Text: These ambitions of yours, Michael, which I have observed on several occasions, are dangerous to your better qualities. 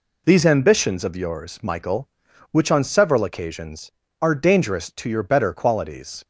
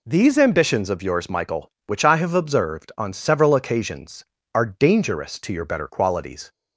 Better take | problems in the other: second | skips "I have observed"; at 2.7 s

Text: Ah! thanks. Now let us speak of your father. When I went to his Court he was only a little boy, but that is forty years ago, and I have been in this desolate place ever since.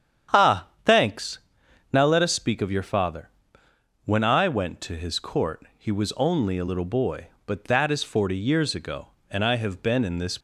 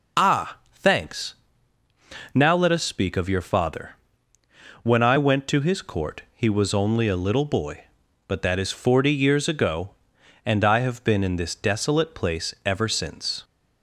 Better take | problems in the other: second | starts louder than the rest; strong; until 2.0 s; 9 dB // stops before "desolate place ever since"; at 10.3 s

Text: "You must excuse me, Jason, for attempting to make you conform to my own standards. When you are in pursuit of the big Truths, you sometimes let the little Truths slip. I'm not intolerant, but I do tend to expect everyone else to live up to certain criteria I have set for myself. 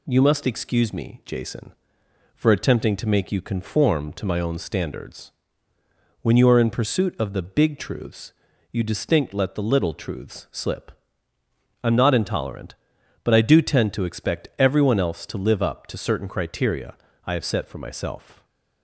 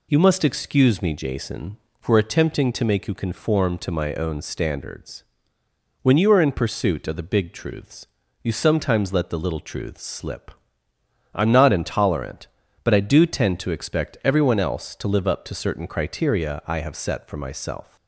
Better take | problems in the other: second | says "distinct" for "sometimes"; at 8.8 s // pauses between "criteria" and "I"; slight; at 16.9 s; 0.30 s long // stays silent after the last word; slight; from 18.3 s on; 0.5 s long

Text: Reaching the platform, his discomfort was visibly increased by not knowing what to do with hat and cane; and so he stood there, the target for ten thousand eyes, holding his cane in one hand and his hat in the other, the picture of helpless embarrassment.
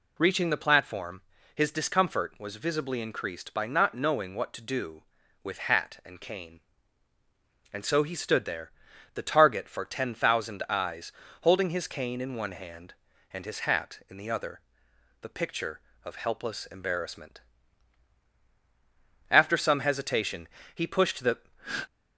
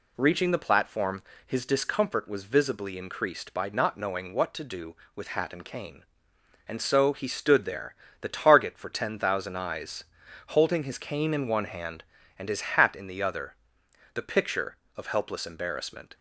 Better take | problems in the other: second | goes on to say "After some hesitation he pushed the"; strong; from 19.2 s on; 2.1 s long

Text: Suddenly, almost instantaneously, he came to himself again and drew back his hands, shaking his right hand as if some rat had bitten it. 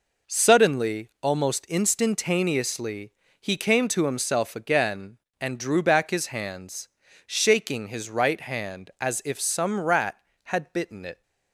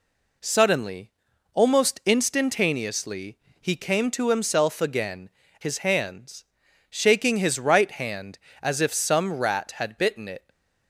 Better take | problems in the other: first | skips "and drew back"; at 5.4 s // stays silent after the last word; slight; from 10.3 s on; 0.5 s long

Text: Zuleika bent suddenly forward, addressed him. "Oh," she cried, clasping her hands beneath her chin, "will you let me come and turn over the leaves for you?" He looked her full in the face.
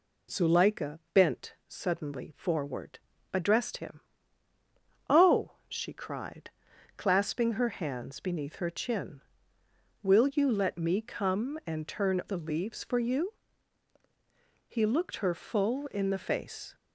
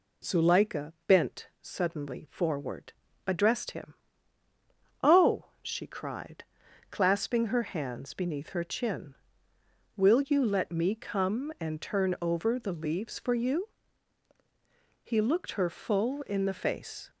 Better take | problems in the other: second | skips "over"; at 12.2 s

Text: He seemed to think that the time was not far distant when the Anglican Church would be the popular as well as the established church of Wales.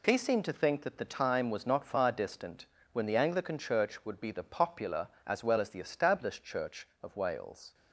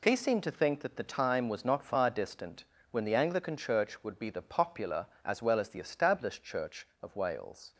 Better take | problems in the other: neither | pauses between "distant" and "when"; slight; the same in both

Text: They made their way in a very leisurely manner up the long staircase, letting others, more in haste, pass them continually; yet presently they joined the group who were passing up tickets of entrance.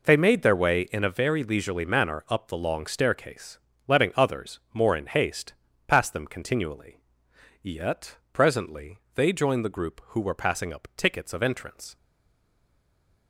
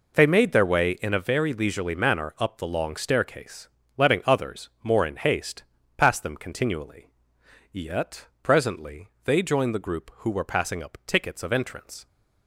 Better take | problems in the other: second | pauses between "yet" and "presently"; slight; at 8.1 s; 0.16 s long; slight in the second // pauses between "presently" and "they"; slight; at 8.9 s; 0.16 s long; slight in the second // stays silent after the last word; noticeable; from 11.9 s on; 1.3 s long

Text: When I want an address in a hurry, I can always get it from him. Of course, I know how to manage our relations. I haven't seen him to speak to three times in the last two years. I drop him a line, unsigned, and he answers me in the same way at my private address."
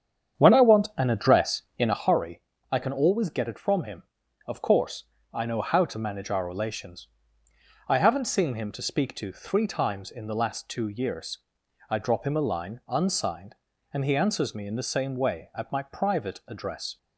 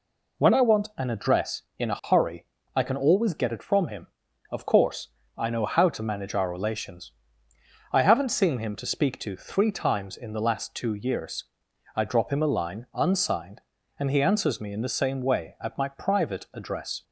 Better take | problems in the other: second | starts louder than the rest; strong; until 2.1 s; 8.5 dB

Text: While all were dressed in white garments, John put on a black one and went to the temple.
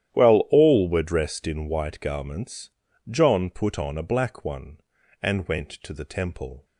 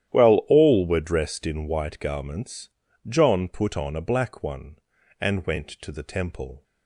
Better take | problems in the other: neither | starts louder than the rest; strong; the same in both

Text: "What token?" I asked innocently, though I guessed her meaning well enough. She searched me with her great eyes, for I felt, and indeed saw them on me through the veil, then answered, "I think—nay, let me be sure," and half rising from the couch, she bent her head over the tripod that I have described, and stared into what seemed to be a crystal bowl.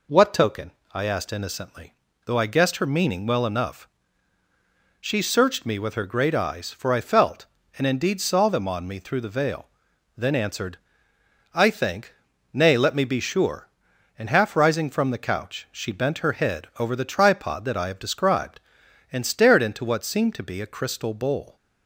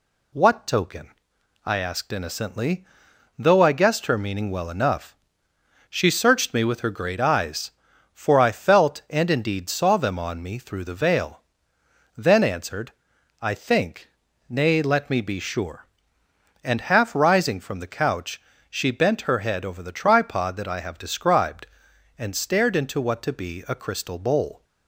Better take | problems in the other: first | skips "seemed"; at 23.2 s

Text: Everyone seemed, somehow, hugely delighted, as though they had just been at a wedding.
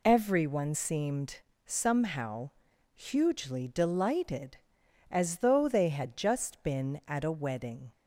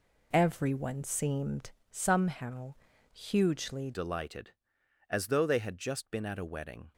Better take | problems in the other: first | changes voice at "delighted"; from 3.9 s on; 3.0 s long

